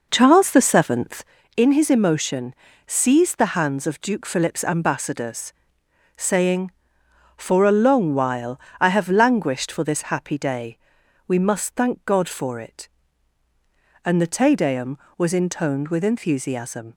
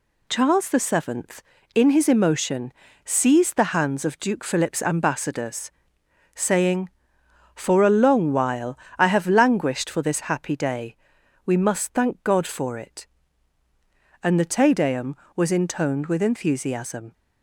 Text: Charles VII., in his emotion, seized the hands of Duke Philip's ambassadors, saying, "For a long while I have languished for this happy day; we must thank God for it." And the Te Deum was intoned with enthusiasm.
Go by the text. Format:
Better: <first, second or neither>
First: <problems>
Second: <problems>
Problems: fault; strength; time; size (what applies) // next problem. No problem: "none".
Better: second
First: starts louder than the rest; noticeable; until 1.4 s; 5 dB // pauses between "while" and "I"; slight; at 8.5 s; 0.22 s long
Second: pauses between "while" and "I"; slight; at 8.7 s; 0.22 s long